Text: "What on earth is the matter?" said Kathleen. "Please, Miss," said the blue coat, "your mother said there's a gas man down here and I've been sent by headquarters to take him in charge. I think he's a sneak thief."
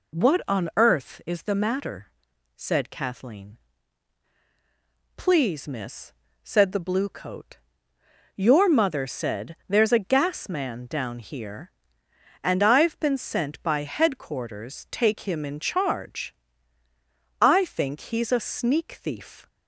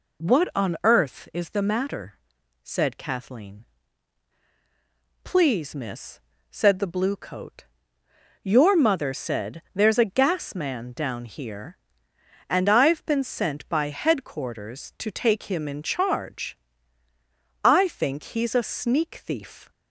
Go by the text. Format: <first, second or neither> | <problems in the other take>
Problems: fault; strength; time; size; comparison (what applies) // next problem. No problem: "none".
second | skips "to"; at 14.8 s